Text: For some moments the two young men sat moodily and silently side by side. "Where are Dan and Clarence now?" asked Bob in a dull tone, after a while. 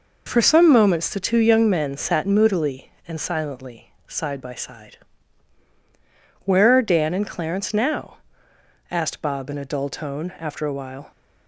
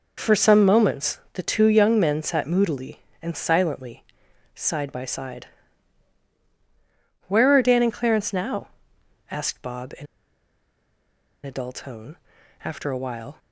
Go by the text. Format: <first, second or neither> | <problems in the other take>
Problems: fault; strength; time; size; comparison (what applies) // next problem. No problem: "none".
first | pauses between "silently" and "side"; noticeable; at 4.0 s; 0.50 s long; slight in the first // pauses between "in" and "a"; strong; at 10.0 s; 1.4 s long